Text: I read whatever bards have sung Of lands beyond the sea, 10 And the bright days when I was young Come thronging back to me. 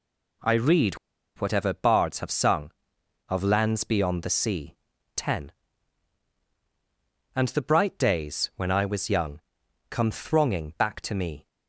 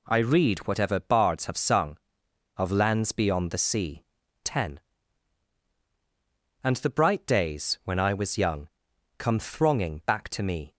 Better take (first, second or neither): second